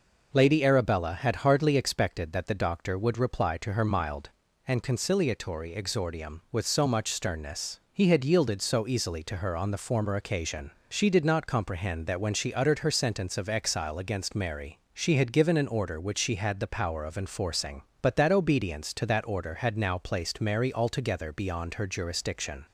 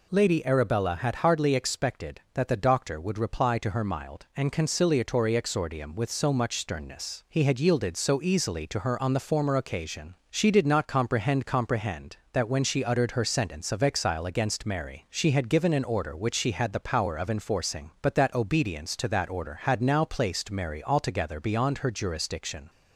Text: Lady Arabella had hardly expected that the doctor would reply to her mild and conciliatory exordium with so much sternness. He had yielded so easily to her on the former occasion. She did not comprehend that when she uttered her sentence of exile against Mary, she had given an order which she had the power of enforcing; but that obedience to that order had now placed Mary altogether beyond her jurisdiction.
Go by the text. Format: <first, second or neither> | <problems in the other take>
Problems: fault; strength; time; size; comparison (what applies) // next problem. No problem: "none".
first | says "comprehend" twice; at 11.4 s